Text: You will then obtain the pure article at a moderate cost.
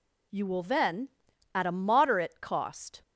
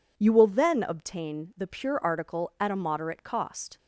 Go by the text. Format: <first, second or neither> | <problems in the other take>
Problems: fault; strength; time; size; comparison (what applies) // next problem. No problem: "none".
second | skips "obtain the pure article"; at 1.3 s